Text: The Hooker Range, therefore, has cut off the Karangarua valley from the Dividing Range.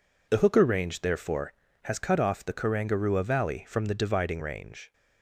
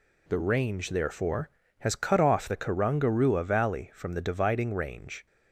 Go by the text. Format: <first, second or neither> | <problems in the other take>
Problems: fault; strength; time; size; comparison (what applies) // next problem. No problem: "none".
first | skips "Hooker"; at 0.3 s